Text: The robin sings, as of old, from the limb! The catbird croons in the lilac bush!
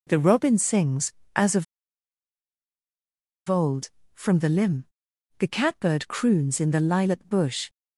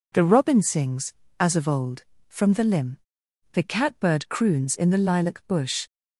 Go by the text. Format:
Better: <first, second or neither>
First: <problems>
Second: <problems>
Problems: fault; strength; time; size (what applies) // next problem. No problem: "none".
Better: second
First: pauses between "of" and "old"; strong; at 1.6 s; 1.8 s long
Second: none